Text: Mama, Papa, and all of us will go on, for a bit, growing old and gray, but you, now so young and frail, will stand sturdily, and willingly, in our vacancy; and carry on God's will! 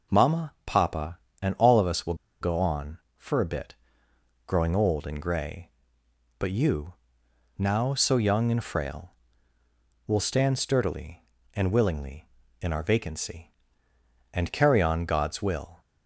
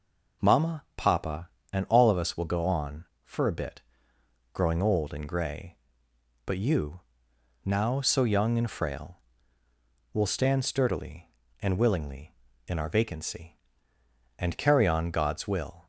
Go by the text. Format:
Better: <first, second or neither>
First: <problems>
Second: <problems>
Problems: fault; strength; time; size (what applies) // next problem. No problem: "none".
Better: second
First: pauses between "will" and "go"; slight; at 2.1 s; 0.26 s long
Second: none